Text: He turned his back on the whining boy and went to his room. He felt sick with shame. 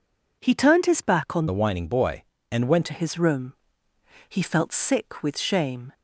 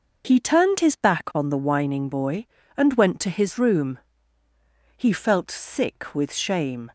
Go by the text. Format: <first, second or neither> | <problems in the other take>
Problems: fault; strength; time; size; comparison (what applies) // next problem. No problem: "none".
second | changes voice from "the" to "went"; from 1.4 to 2.8 s; 1.4 s long